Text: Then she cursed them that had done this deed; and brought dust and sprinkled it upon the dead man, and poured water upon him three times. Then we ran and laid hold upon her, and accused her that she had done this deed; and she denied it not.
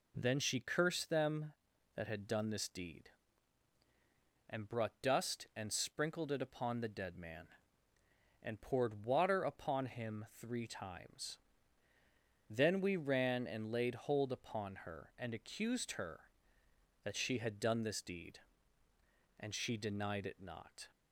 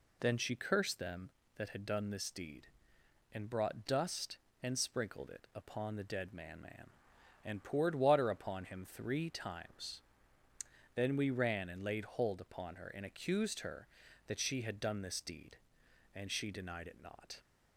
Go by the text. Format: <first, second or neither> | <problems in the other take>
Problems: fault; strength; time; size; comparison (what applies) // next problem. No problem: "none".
first | says "man" twice; at 6.5 s